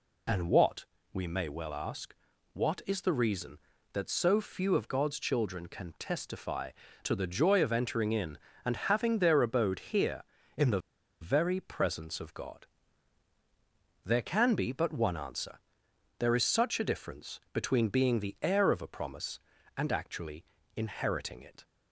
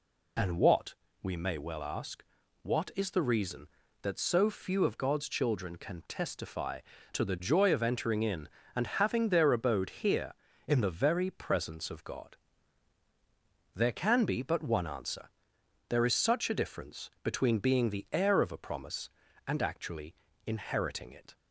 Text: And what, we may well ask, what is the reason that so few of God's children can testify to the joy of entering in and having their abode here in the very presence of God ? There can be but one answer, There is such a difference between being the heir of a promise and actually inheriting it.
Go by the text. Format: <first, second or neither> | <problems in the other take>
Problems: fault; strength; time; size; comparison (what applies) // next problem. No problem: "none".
second | pauses between "the" and "very"; at 10.8 s; 0.40 s long // pauses between "actually" and "inheriting"; slight; at 20.4 s; 0.32 s long; slight in the second